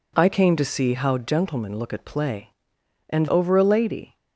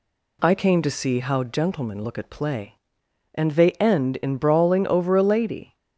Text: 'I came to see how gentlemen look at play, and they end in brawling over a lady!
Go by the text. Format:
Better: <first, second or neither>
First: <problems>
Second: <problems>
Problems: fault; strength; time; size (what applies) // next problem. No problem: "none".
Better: second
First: skips "they end in brawling"; at 3.2 s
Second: none